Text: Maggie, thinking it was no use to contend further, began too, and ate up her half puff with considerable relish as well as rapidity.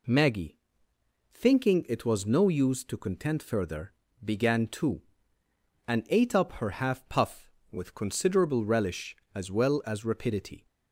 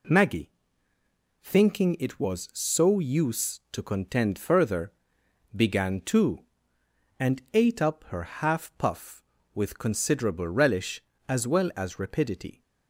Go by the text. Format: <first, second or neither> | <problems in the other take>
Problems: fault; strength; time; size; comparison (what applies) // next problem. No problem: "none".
first | says "so" for "no"; at 2.5 s